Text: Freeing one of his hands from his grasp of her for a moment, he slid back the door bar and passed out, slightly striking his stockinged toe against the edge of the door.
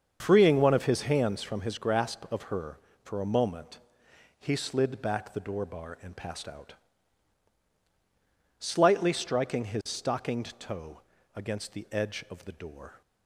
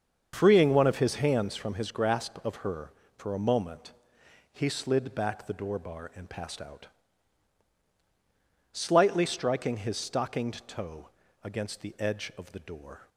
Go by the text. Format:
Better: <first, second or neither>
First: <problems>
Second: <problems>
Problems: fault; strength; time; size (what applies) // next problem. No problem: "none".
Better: neither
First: starts louder than the rest; until 1.2 s; 7 dB // pauses between "toe" and "against"; slight; at 11.0 s; 0.34 s long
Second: starts louder than the rest; until 1.3 s; 7 dB // pauses between "toe" and "against"; slight; at 11.0 s; 0.34 s long